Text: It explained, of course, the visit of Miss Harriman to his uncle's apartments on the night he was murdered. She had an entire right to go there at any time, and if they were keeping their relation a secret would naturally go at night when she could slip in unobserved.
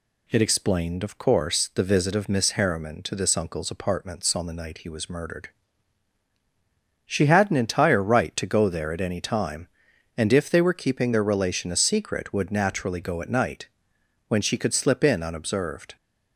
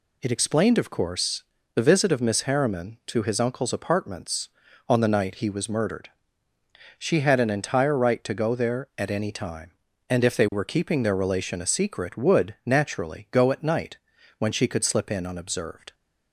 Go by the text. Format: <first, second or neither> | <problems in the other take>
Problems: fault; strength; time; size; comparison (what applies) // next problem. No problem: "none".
second | says "this" for "his"; at 3.1 s // pauses between "night" and "when"; noticeable; at 13.6 s; 0.62 s long; also in the second